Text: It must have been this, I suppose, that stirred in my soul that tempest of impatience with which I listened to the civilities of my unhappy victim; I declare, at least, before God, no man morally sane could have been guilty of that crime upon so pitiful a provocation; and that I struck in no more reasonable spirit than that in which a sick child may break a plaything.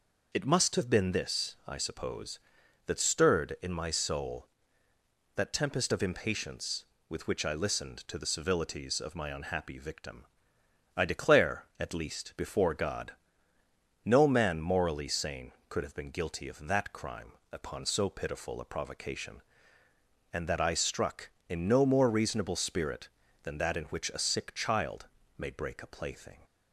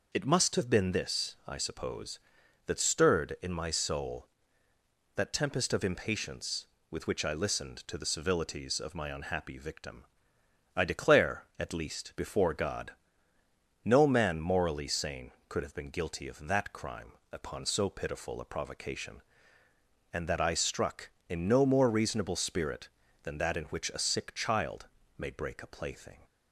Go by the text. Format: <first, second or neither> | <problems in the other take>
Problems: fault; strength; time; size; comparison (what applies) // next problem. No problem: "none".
neither | pauses between "crime" and "upon"; slight; the same in both // pauses between "child" and "may"; slight; the same in both